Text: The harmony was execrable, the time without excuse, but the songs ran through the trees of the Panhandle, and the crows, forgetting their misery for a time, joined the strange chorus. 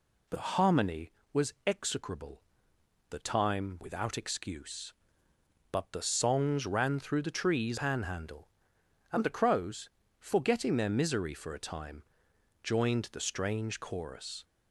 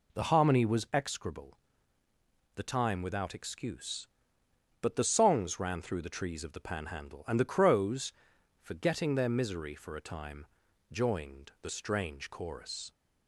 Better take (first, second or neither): second